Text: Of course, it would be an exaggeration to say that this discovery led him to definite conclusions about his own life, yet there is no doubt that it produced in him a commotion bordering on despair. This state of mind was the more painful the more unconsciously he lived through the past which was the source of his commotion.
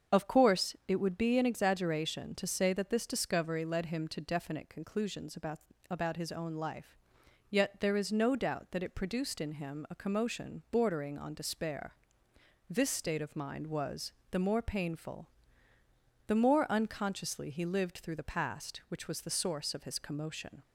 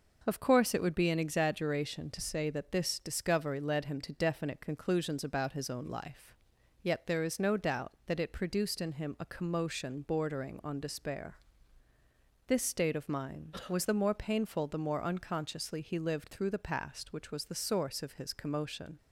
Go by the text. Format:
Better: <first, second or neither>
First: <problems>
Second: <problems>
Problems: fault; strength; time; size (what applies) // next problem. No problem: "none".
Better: second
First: starts louder than the rest; strong; until 1.2 s; 7 dB // says "about" twice; at 5.8 s // pauses between "was" and "the"; slight; at 14.1 s; 0.20 s long // pauses between "painful" and "the"; noticeable; at 15.2 s; 0.98 s long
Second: none